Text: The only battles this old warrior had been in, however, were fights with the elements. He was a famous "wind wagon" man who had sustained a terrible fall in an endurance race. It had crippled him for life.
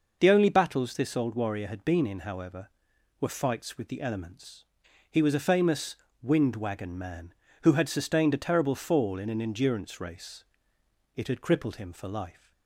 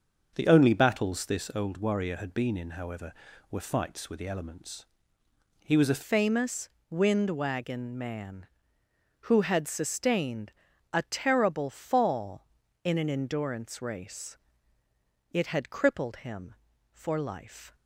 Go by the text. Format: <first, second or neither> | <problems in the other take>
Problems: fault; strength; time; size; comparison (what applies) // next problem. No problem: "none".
first | starts louder than the rest; until 1.3 s; 6.5 dB // changes voice at "famous"; from 6.0 s on; 11.7 s long // pauses between "famous" and "wind"; slight; at 6.6 s; 0.20 s long; slight in the first // pauses between "sustained" and "a"; at 10.5 s; 0.38 s long